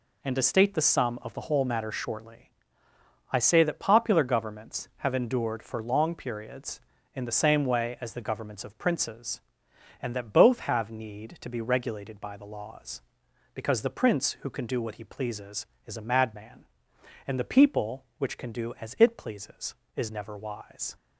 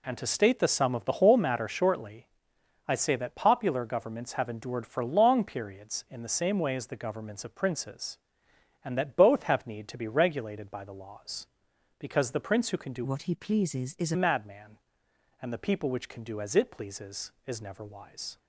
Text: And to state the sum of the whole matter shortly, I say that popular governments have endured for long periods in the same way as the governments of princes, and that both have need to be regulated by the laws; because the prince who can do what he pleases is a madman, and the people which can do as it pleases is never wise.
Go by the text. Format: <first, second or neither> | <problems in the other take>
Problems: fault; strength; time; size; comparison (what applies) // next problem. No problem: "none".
first | changes voice from "what" to "a"; from 13.0 to 14.1 s; 1.1 s long